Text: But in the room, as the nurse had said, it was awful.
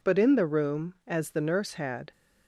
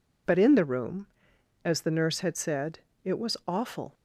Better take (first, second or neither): second